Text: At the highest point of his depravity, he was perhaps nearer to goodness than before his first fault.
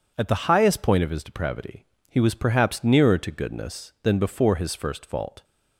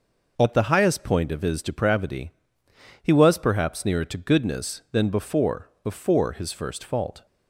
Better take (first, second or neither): first